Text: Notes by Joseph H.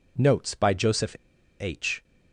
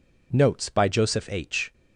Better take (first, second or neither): second